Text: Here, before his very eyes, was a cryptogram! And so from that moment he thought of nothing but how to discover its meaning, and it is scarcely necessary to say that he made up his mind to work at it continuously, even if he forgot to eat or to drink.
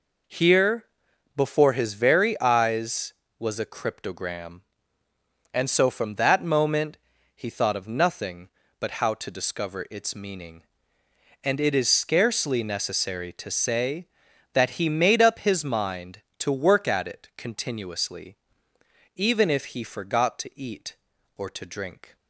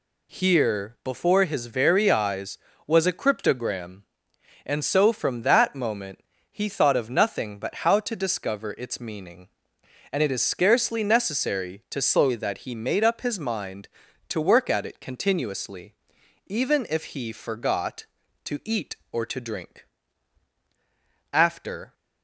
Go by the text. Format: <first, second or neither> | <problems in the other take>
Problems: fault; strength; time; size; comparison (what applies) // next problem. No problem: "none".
first | pauses between "moment" and "he"; slight; at 6.2 s; 0.32 s long; also in the first // goes on to say "After"; from 21.3 s on; 0.60 s long